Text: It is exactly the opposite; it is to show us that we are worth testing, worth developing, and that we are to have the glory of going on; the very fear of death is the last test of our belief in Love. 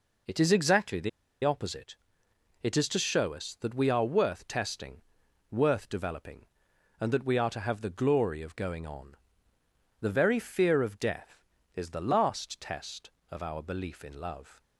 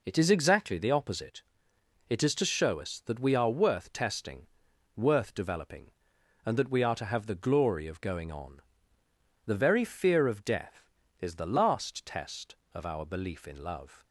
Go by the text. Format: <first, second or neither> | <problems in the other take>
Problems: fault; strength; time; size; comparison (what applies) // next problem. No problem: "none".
second | pauses between "the" and "opposite"; slight; at 1.0 s; 0.35 s long